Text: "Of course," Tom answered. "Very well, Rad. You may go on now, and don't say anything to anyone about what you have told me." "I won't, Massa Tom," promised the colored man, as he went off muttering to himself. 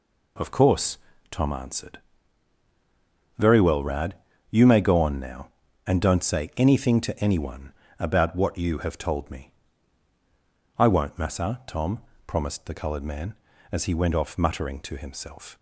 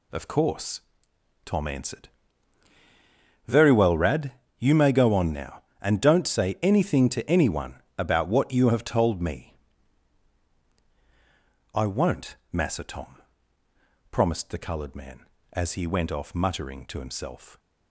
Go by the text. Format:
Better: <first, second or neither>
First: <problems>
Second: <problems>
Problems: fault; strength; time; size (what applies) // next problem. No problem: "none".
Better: neither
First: pauses between "anyone" and "about"; slight; at 7.7 s; 0.26 s long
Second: pauses between "anyone" and "about"; slight; at 7.8 s; 0.16 s long